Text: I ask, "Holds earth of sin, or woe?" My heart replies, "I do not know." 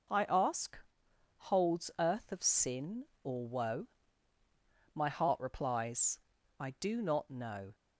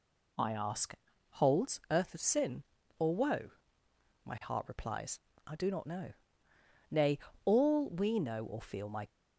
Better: first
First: none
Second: goes on to say "Nay all we know or feel my"; strong; from 6.9 s on; 2.1 s long

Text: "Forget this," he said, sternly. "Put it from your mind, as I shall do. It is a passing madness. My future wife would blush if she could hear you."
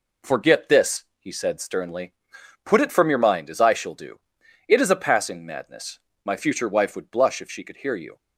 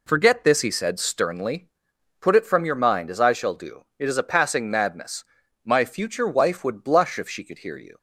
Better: neither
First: none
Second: none

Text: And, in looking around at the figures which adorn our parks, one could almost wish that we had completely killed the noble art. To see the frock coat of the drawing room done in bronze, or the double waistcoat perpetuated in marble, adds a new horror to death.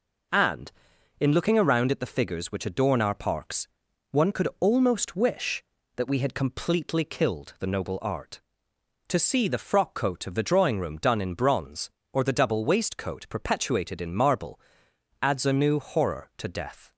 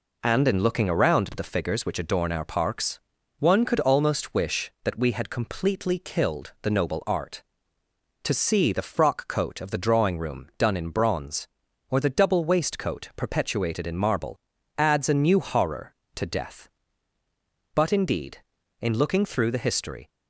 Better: first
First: none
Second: goes on to say "But indeed in looking through the history"; strong; from 17.7 s on; 2.3 s long

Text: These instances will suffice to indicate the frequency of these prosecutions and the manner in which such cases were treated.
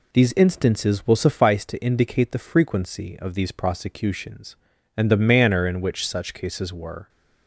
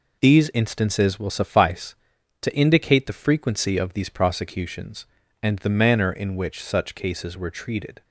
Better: second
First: stops before "treated"; at 7.0 s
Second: none

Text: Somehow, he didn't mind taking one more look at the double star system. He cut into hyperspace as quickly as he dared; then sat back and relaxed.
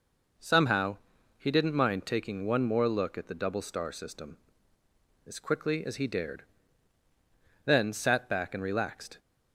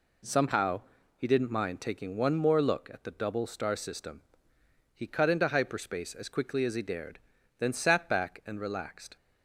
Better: second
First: skips "He cut into hyperspace"; at 4.8 s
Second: none

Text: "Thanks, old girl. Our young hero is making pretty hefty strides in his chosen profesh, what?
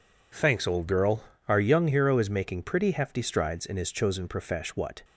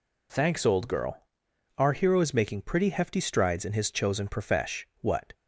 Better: first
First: none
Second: skips "young"; at 1.9 s

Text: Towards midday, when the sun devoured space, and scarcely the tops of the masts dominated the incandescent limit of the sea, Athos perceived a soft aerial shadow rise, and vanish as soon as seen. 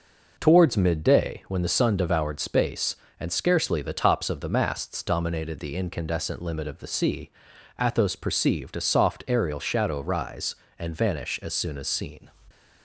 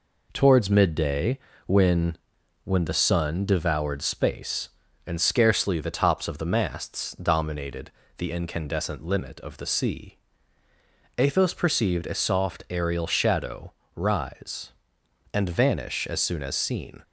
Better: first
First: none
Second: says "when" twice; at 2.6 s // pauses between "dominated" and "the"; slight; at 7.9 s; 0.28 s long // pauses between "shadow" and "rise"; slight; at 13.7 s; 0.24 s long

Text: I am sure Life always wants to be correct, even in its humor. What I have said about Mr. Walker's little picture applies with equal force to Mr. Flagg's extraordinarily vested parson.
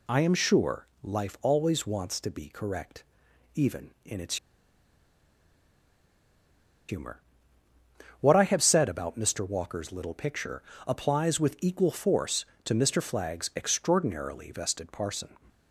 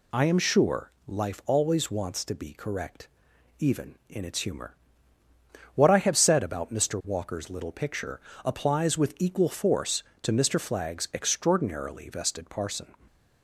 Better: second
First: pauses between "sure" and "Life"; slight; at 0.8 s; 0.20 s long // pauses between "its" and "humor"; strong; at 4.3 s; 2.5 s long // pauses between "picture" and "applies"; slight; at 10.6 s; 0.28 s long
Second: pauses between "sure" and "Life"; slight; at 0.9 s; 0.20 s long // pauses between "picture" and "applies"; slight; at 8.1 s; 0.28 s long

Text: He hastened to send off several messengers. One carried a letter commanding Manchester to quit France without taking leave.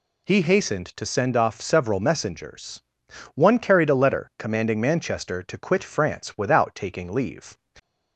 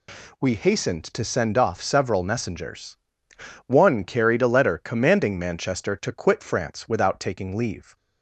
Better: first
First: none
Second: says "We" for "He"; at 0.3 s

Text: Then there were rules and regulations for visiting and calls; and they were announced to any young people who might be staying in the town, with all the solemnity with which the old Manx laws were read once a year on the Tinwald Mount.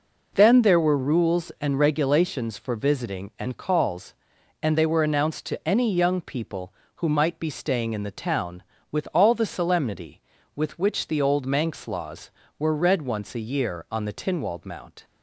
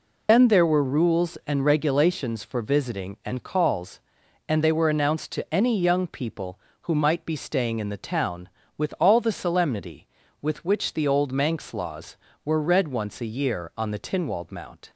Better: first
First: none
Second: loses the start of "Then"; at 0.2 s; 90 ms

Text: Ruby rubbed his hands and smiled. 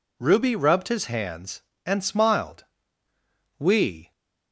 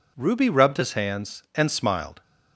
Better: second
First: goes on to say "We"; from 3.5 s on; 0.54 s long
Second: none

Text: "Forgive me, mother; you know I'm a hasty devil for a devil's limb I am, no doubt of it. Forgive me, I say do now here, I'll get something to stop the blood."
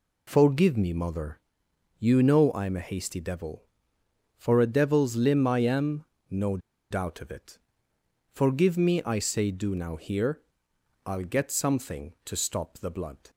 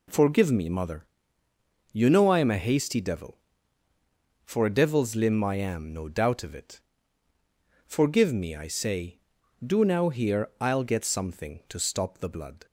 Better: second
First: pauses between "no" and "doubt"; slight; at 6.5 s; 0.32 s long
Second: none

